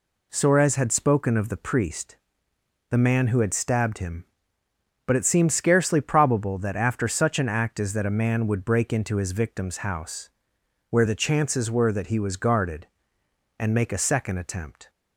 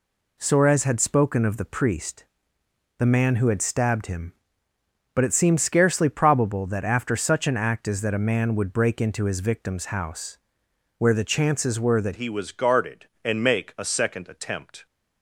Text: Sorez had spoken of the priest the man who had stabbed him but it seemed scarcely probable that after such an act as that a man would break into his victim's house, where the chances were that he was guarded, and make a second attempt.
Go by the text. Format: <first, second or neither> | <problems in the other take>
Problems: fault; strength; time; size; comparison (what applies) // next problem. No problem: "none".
first | pauses between "priest" and "the"; noticeable; at 2.2 s; 0.72 s long; noticeable in the first // changes voice at "he"; from 12.1 s on; 2.7 s long